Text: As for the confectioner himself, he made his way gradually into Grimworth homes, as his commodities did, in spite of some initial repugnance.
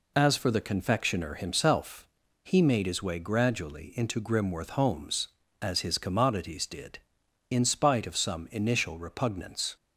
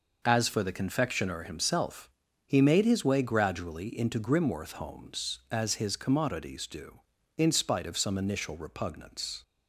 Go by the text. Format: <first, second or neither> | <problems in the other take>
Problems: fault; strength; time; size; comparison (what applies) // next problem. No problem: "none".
first | says "do" for "did"; at 6.6 s